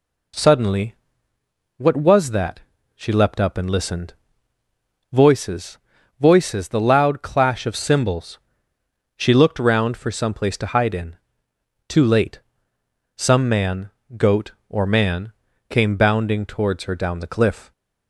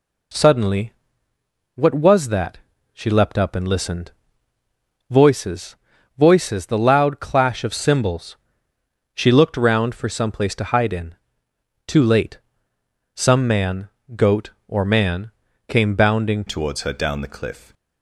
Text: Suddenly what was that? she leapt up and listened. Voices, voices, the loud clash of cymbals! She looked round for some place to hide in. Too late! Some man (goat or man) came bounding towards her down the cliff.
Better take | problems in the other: first | pauses between "Suddenly" and "what"; noticeable; at 0.9 s; 0.82 s long; noticeable in the first // changes voice at "towards"; from 16.4 s on; 1.3 s long

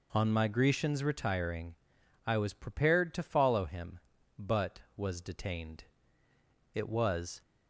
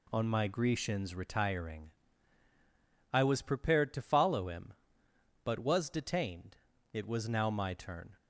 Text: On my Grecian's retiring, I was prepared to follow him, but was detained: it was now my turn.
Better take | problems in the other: second | stops before "now my turn"; at 7.4 s

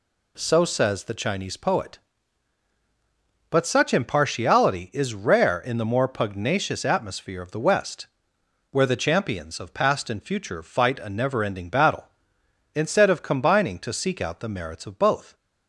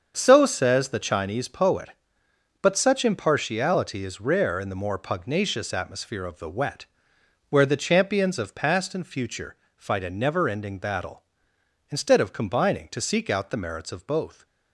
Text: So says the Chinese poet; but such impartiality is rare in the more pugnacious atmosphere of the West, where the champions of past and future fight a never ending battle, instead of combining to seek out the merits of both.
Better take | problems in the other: first | starts louder than the rest; until 1.1 s; 7 dB // says "Wet" for "West"; at 6.4 s // pauses between "future" and "fight"; slight; at 9.5 s; 0.18 s long

